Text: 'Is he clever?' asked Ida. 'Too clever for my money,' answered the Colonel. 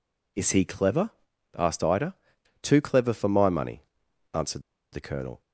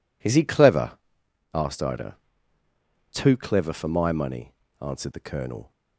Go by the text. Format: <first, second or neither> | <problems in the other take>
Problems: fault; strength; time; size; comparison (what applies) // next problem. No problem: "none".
second | pauses between "answered" and "the"; slight; at 4.6 s; 0.30 s long